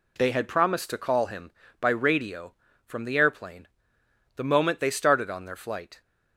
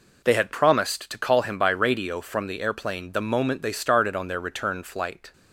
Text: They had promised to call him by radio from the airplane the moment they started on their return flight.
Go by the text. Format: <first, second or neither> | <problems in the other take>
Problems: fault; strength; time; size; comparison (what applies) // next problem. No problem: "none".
second | pauses between "airplane" and "the"; noticeable; at 3.6 s; 0.68 s long // skips "return"; at 5.5 s